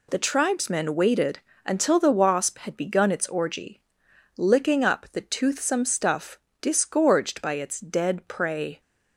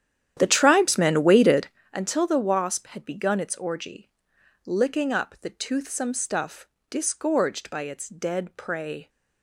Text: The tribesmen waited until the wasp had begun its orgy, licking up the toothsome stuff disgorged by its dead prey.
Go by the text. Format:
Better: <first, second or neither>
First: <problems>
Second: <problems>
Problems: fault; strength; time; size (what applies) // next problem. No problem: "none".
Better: first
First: pauses between "waited" and "until"; slight; at 1.3 s; 0.26 s long // pauses between "stuff" and "disgorged"; slight; at 6.3 s; 0.24 s long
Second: starts louder than the rest; strong; until 1.8 s; 10 dB // pauses between "waited" and "until"; slight; at 1.6 s; 0.25 s long // pauses between "stuff" and "disgorged"; slight; at 6.6 s; 0.24 s long